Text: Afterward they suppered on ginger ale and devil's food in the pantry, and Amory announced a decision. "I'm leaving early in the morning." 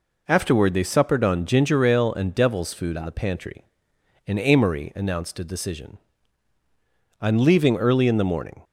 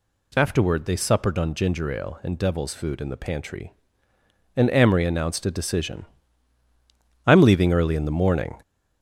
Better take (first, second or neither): first